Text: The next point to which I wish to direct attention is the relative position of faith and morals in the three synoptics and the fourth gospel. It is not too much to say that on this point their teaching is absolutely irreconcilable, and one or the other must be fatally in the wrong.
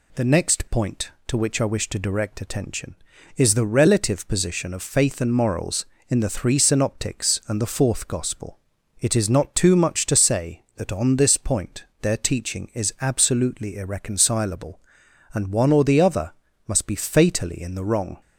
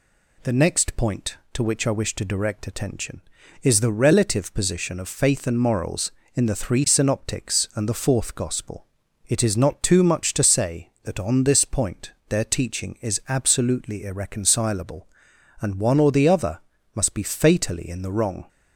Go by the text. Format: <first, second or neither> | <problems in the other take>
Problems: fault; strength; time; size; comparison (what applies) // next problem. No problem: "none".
neither | pauses between "point" and "their"; slight; the same in both // pauses between "other" and "must"; slight; the same in both